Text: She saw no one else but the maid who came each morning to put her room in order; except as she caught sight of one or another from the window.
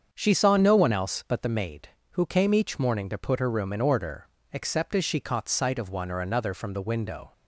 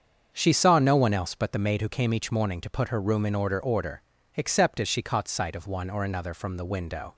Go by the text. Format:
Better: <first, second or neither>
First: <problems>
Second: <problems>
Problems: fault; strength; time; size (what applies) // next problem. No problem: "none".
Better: first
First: starts louder than the rest; until 1.1 s; 7 dB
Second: starts louder than the rest; until 1.3 s; 7 dB // says "order" twice; at 3.6 s